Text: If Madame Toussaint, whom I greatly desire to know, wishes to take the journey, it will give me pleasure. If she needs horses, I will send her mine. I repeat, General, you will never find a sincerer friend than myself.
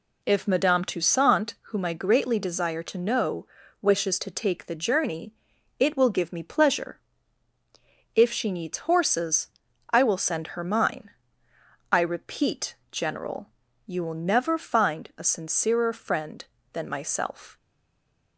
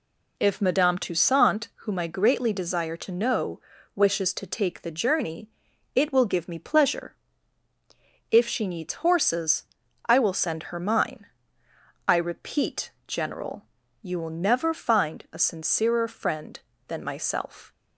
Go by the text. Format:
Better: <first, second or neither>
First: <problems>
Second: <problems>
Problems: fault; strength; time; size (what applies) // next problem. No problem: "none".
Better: second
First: stays silent after the last word; slight; from 17.5 s on; 0.8 s long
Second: none